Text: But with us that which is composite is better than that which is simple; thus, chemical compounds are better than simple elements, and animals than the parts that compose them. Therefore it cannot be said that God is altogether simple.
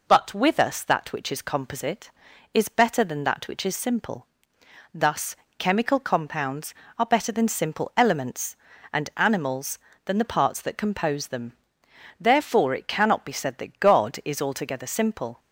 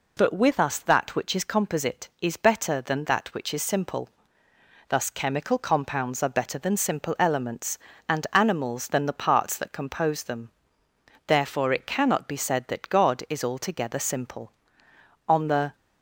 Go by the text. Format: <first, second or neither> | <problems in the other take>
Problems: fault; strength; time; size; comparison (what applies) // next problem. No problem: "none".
first | goes on to say "On the"; slight; from 15.2 s on; 0.46 s long